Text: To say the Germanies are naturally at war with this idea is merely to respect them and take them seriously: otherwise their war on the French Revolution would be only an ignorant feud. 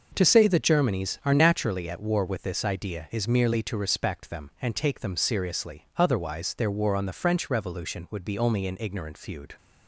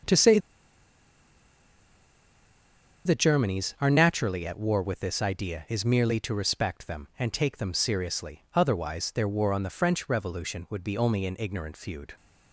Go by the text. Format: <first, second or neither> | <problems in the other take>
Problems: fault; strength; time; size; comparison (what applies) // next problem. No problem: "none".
first | pauses between "say" and "the"; strong; at 0.3 s; 2.6 s long